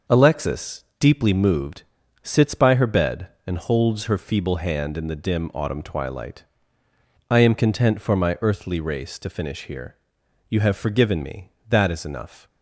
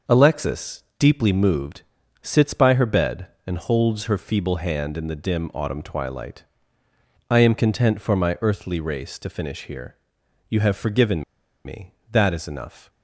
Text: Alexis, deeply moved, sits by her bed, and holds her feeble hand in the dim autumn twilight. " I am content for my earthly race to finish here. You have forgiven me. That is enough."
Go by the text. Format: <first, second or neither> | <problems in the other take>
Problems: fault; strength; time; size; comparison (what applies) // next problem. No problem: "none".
first | pauses between "forgiven" and "me"; at 11.2 s; 0.41 s long